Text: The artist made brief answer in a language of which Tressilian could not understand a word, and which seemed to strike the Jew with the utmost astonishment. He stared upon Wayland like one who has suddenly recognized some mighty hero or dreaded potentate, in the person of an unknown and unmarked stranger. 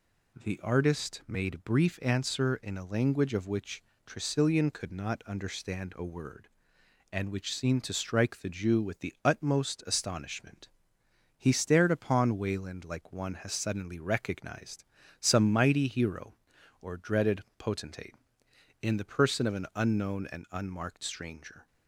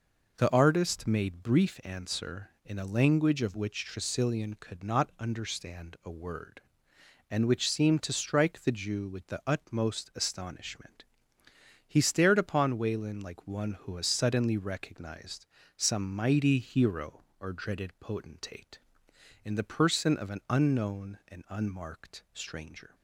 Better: second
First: pauses between "which" and "Tressilian"; slight; at 3.8 s; 0.22 s long // skips "who"; at 13.3 s // pauses between "recognized" and "some"; slight; at 14.8 s; 0.34 s long // pauses between "dreaded" and "potentate"; slight; at 17.4 s; 0.16 s long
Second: pauses between "recognized" and "some"; slight; at 15.4 s; 0.32 s long

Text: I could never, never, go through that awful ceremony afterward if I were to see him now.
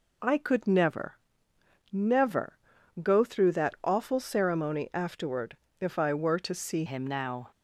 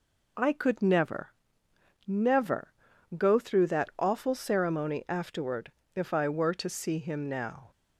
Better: second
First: pauses between "afterward" and "if"; slight; at 5.5 s; 0.24 s long // changes voice at "him"; from 6.8 s on; 0.7 s long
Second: pauses between "afterward" and "if"; slight; at 5.7 s; 0.24 s long

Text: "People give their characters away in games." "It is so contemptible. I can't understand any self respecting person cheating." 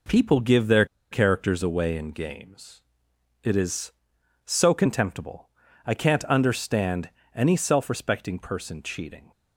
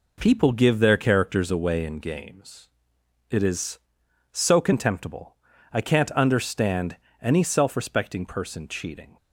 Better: second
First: pauses between "their" and "characters"; slight; at 0.8 s; 0.26 s long // pauses between "understand" and "any"; slight; at 7.0 s; 0.26 s long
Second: pauses between "understand" and "any"; slight; at 6.9 s; 0.26 s long

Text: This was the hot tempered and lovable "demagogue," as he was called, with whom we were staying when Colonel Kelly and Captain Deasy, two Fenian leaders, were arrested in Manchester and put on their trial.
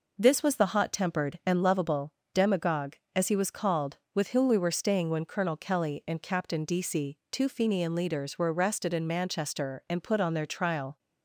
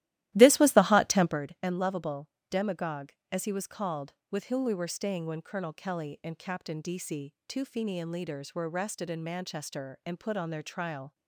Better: first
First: pauses between "lovable" and "demagogue"; slight; at 2.1 s; 0.18 s long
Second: starts louder than the rest; strong; until 1.4 s; 15 dB // pauses between "lovable" and "demagogue"; slight; at 2.3 s; 0.18 s long

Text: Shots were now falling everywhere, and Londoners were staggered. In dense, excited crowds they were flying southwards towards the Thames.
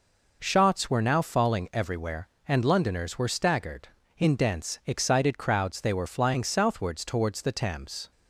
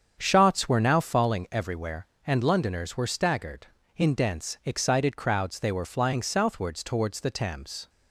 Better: first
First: none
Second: starts louder than the rest; strong; until 1.4 s; 7.5 dB

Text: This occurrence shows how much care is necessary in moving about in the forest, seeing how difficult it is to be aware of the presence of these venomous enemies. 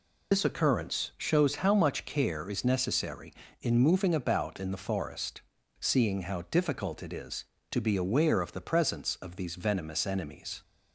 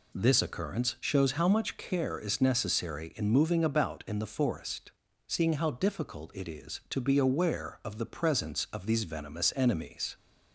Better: second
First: loses the start of "This"; at 0.3 s; 60 ms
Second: none

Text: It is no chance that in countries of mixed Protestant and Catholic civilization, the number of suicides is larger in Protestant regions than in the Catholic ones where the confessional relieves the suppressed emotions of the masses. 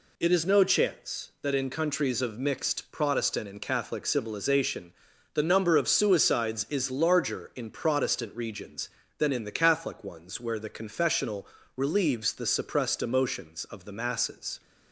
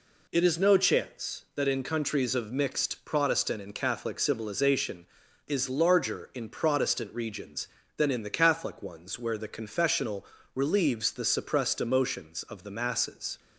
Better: first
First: pauses between "confessional" and "relieves"; slight; at 11.4 s; 0.28 s long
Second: skips "the number of suicides"; at 5.2 s // pauses between "confessional" and "relieves"; slight; at 10.2 s; 0.28 s long

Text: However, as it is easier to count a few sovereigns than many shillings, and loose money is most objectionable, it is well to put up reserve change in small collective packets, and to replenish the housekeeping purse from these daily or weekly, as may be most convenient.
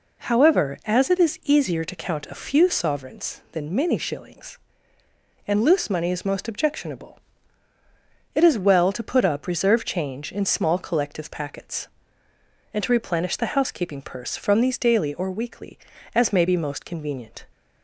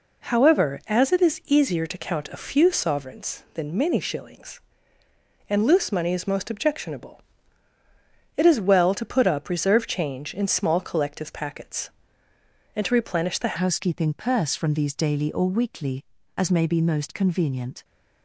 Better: first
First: none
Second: changes voice at "housekeeping"; from 13.6 s on; 4.2 s long

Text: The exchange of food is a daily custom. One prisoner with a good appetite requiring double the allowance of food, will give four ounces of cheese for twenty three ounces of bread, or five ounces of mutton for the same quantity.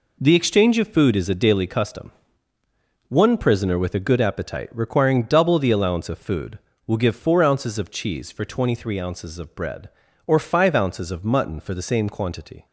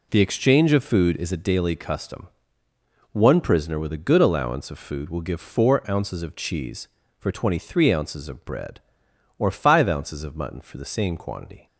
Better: first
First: none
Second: skips "appetite requiring double the"; at 4.1 s

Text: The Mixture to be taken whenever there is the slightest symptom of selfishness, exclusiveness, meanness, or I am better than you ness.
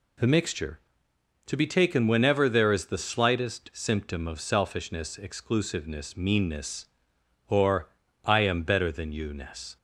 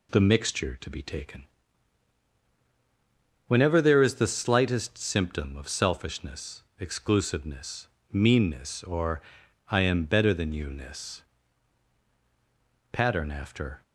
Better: first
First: pauses between "or" and "I"; slight; at 7.8 s; 0.36 s long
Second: pauses between "taken" and "whenever"; strong; at 1.4 s; 2.0 s long // pauses between "or" and "I"; noticeable; at 9.2 s; 0.48 s long // goes on to say "Pattern after"; noticeable; from 12.9 s on; 0.90 s long

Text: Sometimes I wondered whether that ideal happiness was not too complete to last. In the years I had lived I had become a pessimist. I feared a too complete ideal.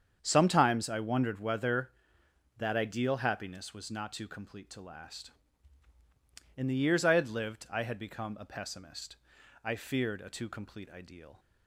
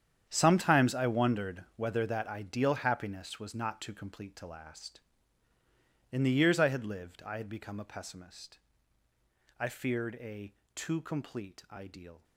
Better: first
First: starts louder than the rest; strong; until 1.2 s; 8 dB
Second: gets quieter; strong; throughout; 14.5 dB // starts louder than the rest; strong; until 1.3 s; 9 dB // pauses between "a" and "too"; slight; at 10.5 s; 0.22 s long

